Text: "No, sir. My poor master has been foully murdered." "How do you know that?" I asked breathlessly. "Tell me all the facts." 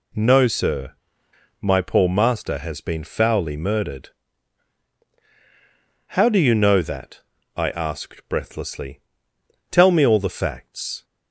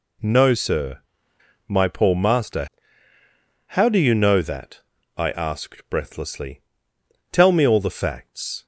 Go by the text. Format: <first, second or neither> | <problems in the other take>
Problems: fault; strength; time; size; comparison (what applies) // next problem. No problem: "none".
first | skips "has been foully murdered"; at 3.1 s